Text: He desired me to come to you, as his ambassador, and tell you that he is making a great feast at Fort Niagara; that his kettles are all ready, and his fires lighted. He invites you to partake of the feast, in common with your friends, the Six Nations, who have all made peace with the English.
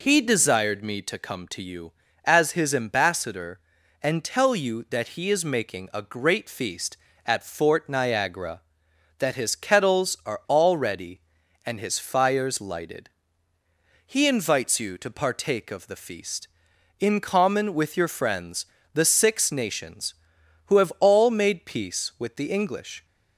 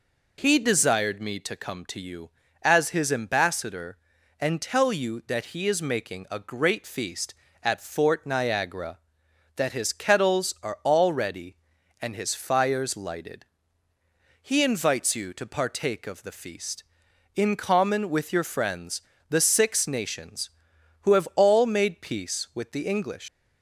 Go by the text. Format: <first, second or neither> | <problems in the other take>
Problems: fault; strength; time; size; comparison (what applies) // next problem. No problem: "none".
first | leaves "English" unfinished; at 23.2 s; 125 ms